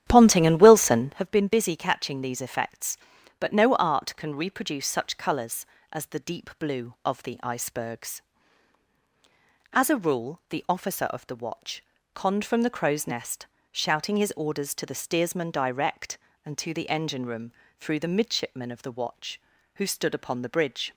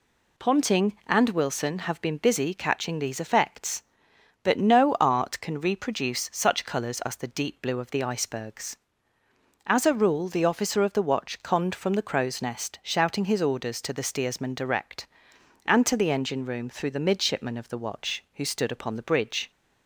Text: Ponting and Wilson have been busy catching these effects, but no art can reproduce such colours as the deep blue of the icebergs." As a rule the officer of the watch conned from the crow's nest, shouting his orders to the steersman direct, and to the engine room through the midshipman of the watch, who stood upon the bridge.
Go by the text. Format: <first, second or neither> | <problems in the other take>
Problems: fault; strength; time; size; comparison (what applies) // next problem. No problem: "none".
second | starts louder than the rest; strong; until 1.3 s; 10 dB // pauses between "watch" and "conned"; slight; at 11.8 s; 0.30 s long // pauses between "room" and "through"; slight; at 17.5 s; 0.26 s long